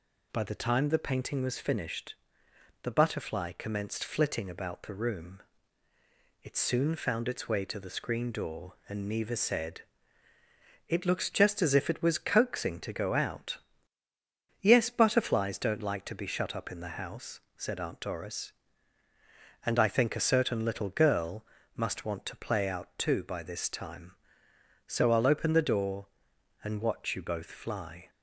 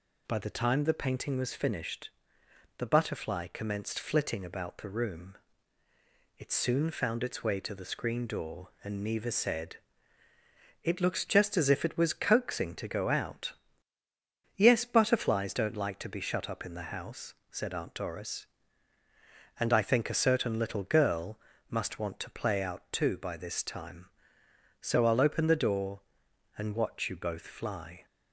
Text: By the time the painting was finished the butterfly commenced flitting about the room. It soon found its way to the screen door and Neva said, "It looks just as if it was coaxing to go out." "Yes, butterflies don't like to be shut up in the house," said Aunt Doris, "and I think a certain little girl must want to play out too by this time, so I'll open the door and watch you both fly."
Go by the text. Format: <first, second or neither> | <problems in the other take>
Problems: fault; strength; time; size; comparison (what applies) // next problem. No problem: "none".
neither | pauses between "finished" and "the"; noticeable; the same in both // pauses between "girl" and "must"; slight; the same in both